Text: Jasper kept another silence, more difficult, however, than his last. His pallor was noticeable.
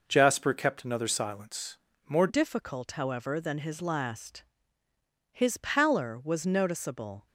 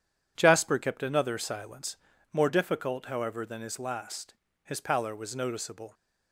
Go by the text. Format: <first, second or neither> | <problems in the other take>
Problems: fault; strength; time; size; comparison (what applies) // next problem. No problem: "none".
second | changes voice at "difficult"; from 2.2 s on; 5.0 s long